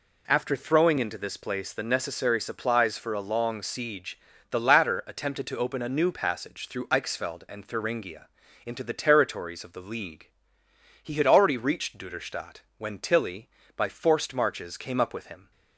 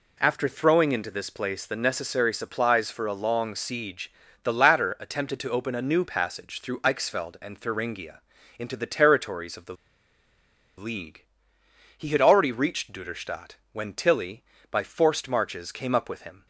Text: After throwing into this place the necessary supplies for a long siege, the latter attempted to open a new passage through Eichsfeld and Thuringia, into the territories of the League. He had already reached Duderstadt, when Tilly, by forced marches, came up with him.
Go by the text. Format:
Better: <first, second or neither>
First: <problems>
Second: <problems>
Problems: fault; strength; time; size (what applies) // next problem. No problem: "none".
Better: first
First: none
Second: pauses between "the" and "League"; at 9.7 s; 1.0 s long